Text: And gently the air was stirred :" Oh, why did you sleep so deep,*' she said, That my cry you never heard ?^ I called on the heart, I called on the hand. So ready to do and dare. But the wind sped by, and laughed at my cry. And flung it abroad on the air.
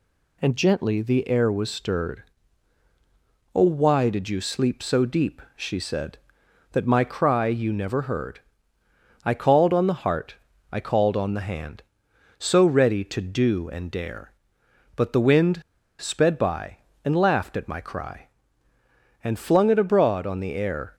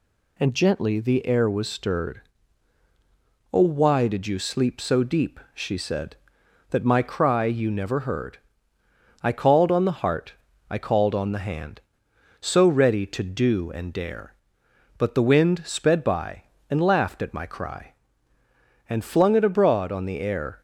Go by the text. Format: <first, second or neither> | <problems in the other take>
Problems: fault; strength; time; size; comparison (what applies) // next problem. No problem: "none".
second | pauses between "wind" and "sped"; at 15.6 s; 0.40 s long